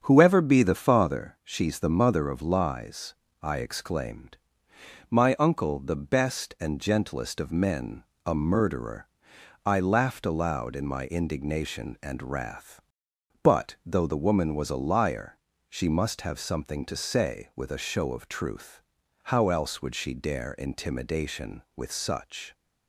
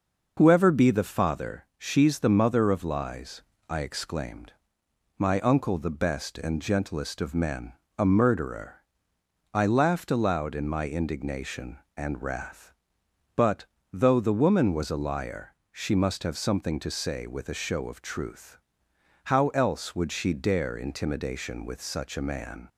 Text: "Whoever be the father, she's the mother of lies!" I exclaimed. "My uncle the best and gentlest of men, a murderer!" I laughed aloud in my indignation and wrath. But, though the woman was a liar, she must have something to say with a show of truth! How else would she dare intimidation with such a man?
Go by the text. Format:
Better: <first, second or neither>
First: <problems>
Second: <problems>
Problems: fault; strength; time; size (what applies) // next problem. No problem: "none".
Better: second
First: starts louder than the rest; strong; until 1.0 s; 7.5 dB // stops before "a man"; at 22.5 s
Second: none